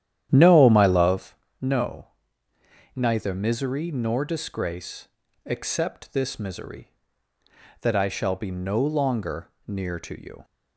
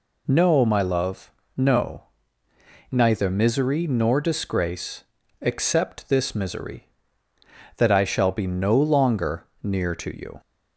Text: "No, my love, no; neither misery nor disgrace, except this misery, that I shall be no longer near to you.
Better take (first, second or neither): second